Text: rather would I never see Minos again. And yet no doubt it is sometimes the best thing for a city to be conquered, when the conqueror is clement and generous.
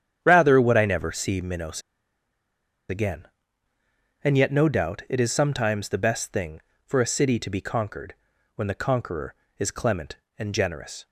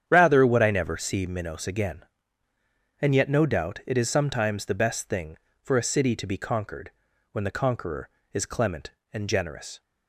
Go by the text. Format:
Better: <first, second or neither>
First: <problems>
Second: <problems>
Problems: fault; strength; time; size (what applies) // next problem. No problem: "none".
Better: second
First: starts louder than the rest; strong; until 1.2 s; 9 dB // pauses between "Minos" and "again"; at 1.8 s; 1.0 s long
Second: starts louder than the rest; strong; until 1.0 s; 9 dB